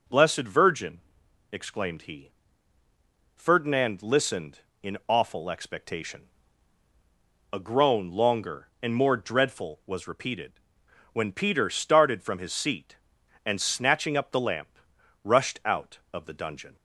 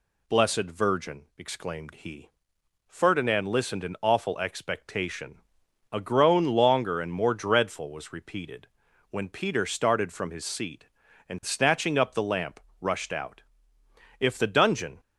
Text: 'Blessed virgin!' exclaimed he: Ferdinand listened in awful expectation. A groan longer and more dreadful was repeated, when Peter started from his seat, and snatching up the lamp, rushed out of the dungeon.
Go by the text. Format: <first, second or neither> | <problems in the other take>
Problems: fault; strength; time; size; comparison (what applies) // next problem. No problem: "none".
first | says "if" for "of"; at 14.2 s